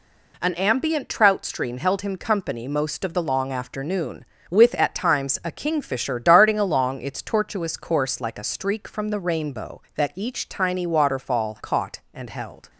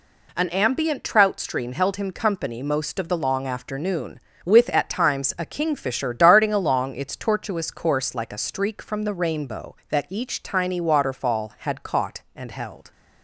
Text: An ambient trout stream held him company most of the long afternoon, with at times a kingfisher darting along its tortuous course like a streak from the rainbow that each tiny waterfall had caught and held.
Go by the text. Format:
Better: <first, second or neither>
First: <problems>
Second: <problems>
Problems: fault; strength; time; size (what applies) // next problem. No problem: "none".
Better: second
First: skips "had"; at 11.6 s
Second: none